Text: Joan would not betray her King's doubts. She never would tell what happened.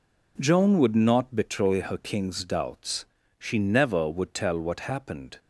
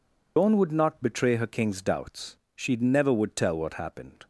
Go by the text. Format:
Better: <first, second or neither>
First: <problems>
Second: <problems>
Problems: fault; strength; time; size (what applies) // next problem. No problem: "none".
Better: first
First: none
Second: loses the start of "Joan"; at 0.3 s; 140 ms